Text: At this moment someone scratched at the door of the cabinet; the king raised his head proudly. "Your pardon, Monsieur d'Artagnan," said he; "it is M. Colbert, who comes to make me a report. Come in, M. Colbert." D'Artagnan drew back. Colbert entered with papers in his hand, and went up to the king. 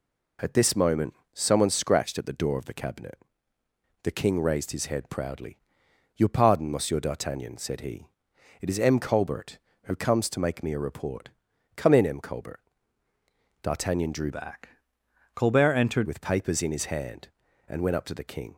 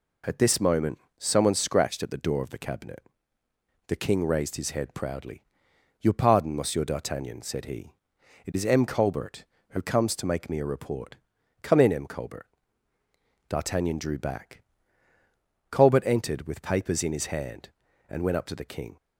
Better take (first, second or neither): second